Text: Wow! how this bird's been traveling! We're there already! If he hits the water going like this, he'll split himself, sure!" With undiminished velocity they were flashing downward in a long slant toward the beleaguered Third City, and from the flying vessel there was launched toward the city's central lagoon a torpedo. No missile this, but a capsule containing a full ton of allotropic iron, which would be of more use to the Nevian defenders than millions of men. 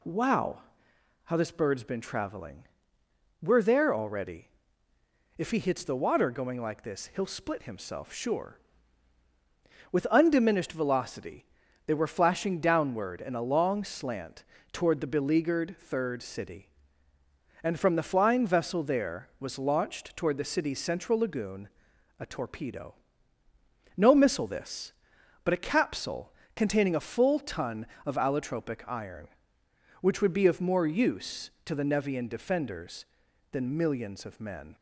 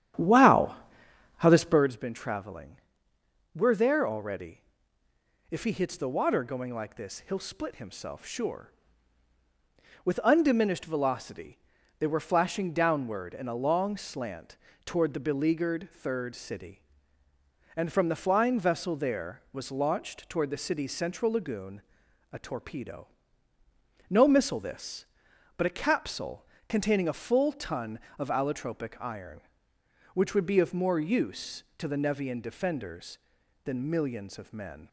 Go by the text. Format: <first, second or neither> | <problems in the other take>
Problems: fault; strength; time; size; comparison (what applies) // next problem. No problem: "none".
first | starts louder than the rest; strong; until 1.9 s; 10.5 dB // pauses between "velocity" and "they"; at 11.5 s; 0.40 s long; also in the first // pauses between "slant" and "toward"; slight; at 14.5 s; 0.28 s long; slight in the first // pauses between "lagoon" and "a"; noticeable; at 21.8 s; 0.50 s long; noticeable in the first // pauses between "capsule" and "containing"; slight; at 26.4 s; 0.24 s long; slight in the first